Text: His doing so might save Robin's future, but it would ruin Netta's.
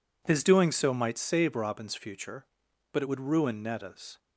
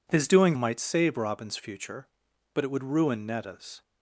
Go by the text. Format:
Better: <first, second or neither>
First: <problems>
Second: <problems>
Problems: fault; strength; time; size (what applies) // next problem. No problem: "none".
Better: first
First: none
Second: skips "so"; at 0.5 s